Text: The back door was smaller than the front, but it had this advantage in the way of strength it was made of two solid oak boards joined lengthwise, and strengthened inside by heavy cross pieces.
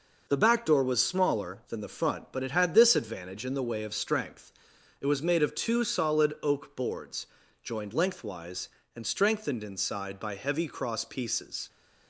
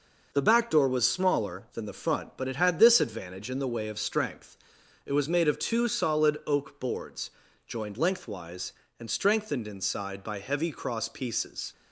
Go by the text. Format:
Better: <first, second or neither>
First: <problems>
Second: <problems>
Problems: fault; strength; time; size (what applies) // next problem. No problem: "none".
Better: neither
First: pauses between "strength" and "it"; noticeable; at 4.5 s; 0.48 s long // pauses between "boards" and "joined"; slight; at 7.2 s; 0.36 s long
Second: pauses between "strength" and "it"; noticeable; at 4.5 s; 0.48 s long // pauses between "boards" and "joined"; slight; at 7.2 s; 0.36 s long